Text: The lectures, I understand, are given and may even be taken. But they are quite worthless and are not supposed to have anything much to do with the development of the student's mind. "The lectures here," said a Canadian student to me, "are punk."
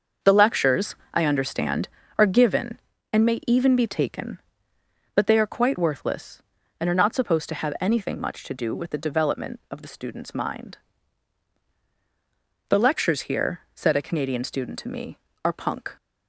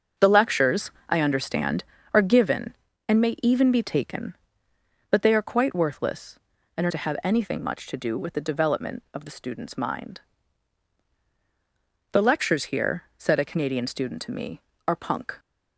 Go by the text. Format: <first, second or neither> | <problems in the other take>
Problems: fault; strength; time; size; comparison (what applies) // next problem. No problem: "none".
first | starts louder than the rest; until 1.3 s; 6.5 dB; also in the first // skips "not supposed"; at 6.9 s